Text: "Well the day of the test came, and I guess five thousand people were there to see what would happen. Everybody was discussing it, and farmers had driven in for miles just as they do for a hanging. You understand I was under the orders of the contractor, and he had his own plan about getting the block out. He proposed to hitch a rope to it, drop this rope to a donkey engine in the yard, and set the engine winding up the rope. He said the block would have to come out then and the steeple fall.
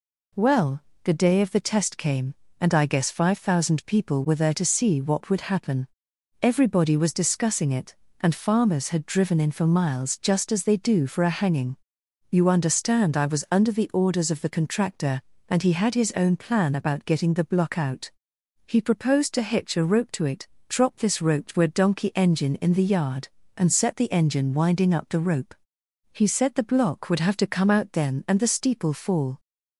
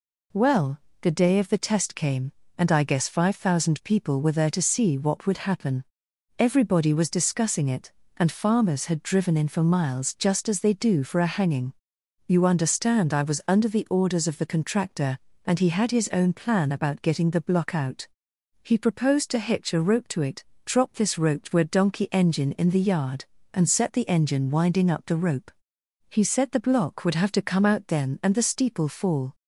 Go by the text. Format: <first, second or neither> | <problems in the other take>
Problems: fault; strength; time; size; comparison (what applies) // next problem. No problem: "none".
neither | pauses between "Well" and "the"; slight; the same in both